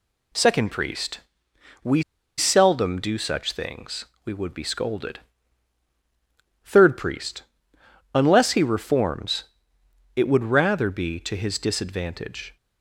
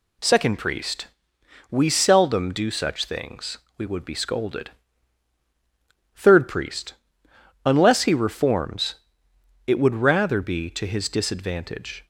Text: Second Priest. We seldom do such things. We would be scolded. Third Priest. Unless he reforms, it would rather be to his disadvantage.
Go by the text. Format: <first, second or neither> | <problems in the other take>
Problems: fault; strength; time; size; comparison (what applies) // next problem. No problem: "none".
second | pauses between "We" and "seldom"; slight; at 2.0 s; 0.36 s long